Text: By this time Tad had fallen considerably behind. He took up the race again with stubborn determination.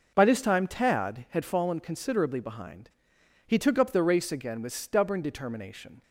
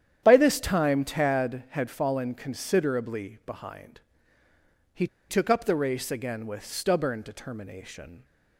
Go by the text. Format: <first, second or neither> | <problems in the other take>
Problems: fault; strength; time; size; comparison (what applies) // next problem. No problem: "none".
first | starts louder than the rest; strong; until 1.2 s; 9.5 dB // pauses between "He" and "took"; slight; at 5.0 s; 0.22 s long